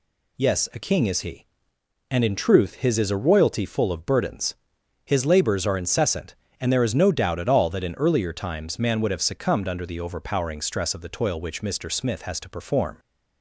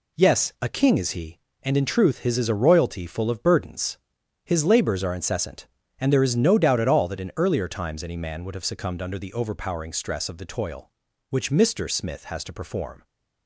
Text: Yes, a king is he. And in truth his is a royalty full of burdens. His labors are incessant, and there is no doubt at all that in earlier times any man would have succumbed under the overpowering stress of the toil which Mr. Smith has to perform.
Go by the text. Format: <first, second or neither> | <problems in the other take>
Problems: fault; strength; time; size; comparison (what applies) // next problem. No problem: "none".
second | skips "any"; at 8.7 s